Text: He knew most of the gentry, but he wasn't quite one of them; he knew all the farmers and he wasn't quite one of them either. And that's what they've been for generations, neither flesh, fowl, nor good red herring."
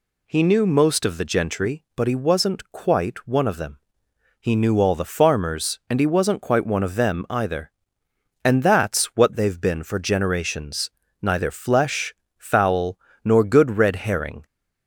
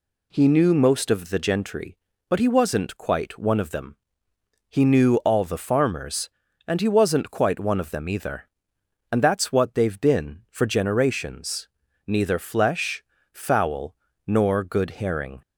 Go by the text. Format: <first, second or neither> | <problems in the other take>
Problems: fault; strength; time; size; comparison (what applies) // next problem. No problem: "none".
first | skips "red"; at 15.0 s